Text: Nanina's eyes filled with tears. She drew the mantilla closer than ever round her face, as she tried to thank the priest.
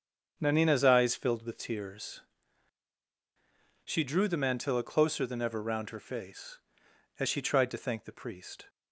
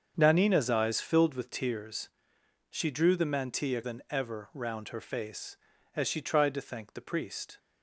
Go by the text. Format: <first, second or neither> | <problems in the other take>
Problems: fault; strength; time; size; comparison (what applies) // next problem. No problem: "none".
first | starts louder than the rest; strong; until 1.1 s; 7 dB; strong in the first // skips "closer"; at 3.8 s